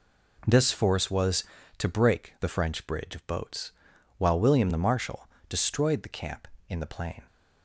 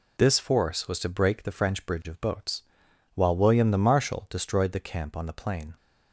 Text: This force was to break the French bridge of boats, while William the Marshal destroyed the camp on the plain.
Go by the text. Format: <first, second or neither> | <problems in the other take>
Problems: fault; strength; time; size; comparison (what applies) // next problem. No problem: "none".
second | pauses between "Marshal" and "destroyed"; slight; at 5.2 s; 0.22 s long // says "in" for "on"; at 6.6 s